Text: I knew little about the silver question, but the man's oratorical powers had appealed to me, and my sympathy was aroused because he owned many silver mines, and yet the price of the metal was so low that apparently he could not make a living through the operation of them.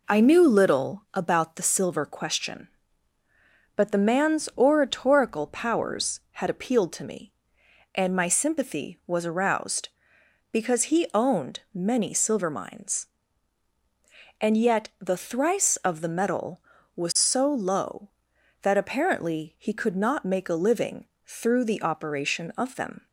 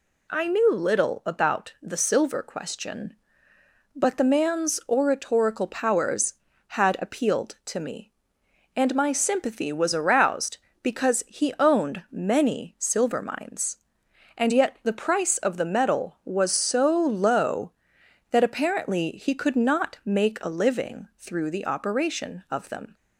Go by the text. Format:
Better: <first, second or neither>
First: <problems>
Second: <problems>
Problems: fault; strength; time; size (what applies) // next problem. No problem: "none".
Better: second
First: says "thrice" for "price"; at 15.1 s // pauses between "living" and "through"; slight; at 21.0 s; 0.20 s long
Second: none